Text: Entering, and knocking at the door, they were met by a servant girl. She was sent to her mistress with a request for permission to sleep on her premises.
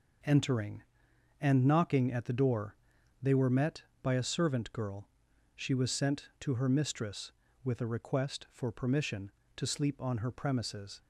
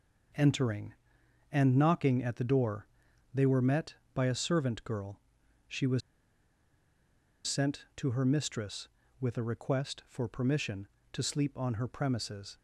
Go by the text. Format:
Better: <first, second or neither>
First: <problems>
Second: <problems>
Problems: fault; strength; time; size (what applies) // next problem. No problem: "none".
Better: first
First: none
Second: pauses between "was" and "sent"; strong; at 6.0 s; 1.4 s long